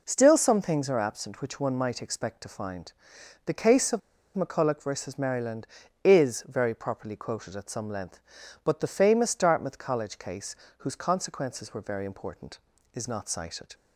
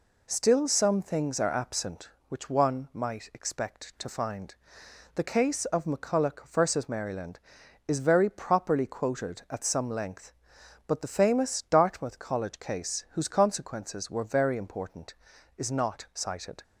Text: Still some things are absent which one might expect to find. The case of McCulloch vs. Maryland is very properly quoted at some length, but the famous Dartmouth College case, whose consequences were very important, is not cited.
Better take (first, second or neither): second